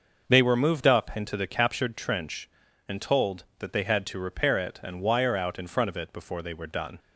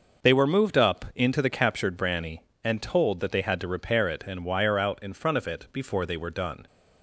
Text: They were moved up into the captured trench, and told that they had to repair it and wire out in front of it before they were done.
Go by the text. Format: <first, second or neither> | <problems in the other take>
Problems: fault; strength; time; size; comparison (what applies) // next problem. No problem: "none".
first | says "branny" for "trench"; at 1.9 s